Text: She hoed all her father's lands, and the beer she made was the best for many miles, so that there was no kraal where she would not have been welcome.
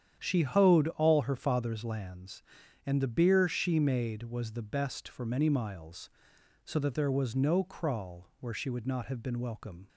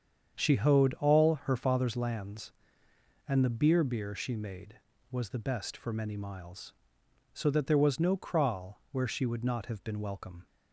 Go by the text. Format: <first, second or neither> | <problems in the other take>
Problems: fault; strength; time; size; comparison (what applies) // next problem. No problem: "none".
first | starts louder than the rest; strong; until 1.5 s; 8 dB; strong in the first // says "beer" twice; at 3.8 s